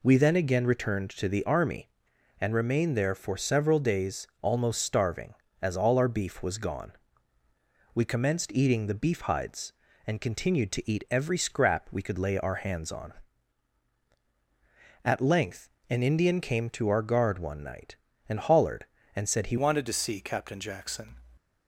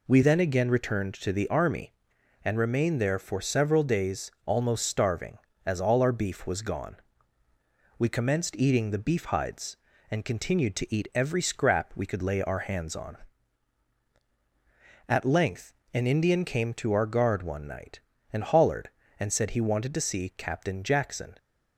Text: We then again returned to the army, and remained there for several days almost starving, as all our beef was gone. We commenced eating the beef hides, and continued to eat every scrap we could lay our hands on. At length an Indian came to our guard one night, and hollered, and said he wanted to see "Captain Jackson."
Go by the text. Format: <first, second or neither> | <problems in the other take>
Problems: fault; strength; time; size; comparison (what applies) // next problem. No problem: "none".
second | pauses between "length" and "an"; slight; at 15.6 s; 0.20 s long; slight in the second // changes voice at "wanted"; from 19.5 s on; 1.6 s long